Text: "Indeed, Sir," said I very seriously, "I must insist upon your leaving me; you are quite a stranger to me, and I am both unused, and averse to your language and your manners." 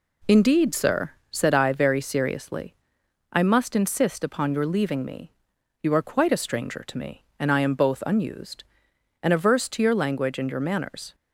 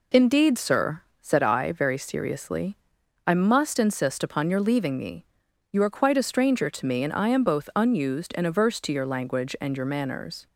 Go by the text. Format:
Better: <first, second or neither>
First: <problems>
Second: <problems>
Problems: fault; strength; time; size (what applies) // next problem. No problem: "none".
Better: neither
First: none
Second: none